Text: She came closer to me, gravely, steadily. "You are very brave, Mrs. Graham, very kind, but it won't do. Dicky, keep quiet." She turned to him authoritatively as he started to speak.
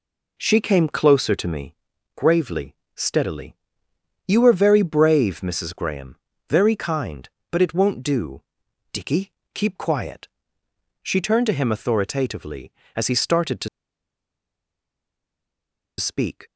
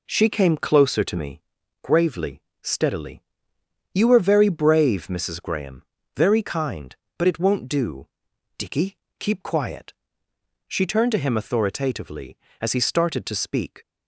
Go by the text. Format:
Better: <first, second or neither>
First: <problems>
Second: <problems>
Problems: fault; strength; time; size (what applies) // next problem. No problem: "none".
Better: second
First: pauses between "to" and "speak"; strong; at 13.6 s; 2.3 s long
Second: none